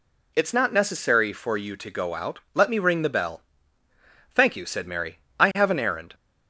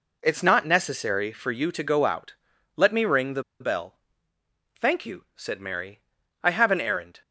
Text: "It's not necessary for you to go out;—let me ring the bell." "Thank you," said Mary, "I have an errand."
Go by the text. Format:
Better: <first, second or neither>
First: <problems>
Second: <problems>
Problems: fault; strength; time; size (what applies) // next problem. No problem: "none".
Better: first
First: none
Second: pauses between "the" and "bell"; slight; at 3.4 s; 0.18 s long